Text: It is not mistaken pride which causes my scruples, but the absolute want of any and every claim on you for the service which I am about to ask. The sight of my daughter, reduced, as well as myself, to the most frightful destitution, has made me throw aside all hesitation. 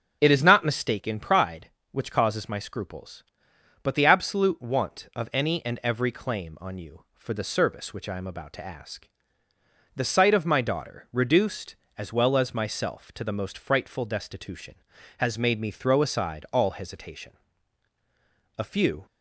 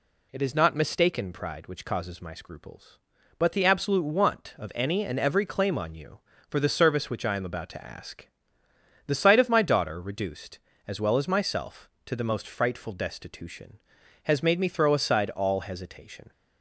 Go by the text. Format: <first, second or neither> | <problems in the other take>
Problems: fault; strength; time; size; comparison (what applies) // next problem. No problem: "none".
second | starts louder than the rest; until 1.2 s; 6.5 dB // goes on to say "A few"; slight; from 18.5 s on; 0.48 s long